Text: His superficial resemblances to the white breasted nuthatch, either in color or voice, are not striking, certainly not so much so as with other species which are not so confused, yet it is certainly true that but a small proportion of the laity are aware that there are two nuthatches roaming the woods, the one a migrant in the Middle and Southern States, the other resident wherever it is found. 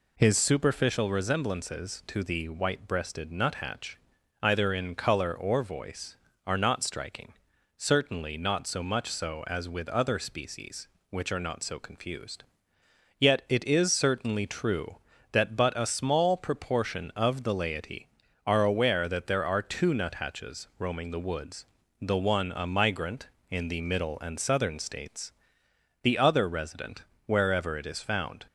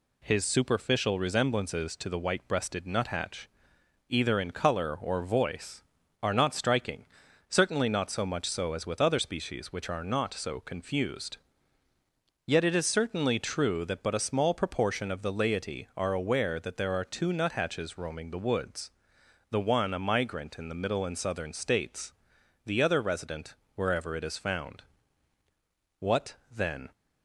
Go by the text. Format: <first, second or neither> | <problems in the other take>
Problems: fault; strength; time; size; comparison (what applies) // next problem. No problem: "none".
first | pauses between "resident" and "wherever"; slight; at 23.5 s; 0.18 s long; slight in the first // goes on to say "What then"; noticeable; from 25.9 s on; 0.94 s long